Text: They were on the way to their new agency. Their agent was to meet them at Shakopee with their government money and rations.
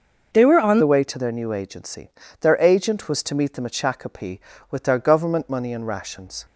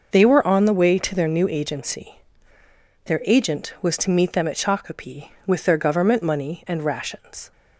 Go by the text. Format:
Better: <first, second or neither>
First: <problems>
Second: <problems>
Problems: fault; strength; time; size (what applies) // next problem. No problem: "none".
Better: second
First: changes voice at "the"; from 0.8 s on; 5.6 s long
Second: none